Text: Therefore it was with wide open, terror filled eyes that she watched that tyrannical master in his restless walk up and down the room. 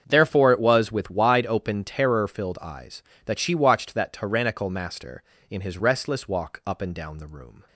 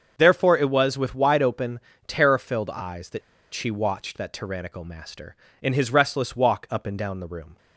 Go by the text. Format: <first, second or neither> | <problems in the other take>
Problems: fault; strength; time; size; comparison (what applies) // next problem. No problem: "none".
first | starts louder than the rest; until 1.1 s; 6.5 dB; strong in the first // pauses between "that" and "she"; slight; at 3.2 s; 0.33 s long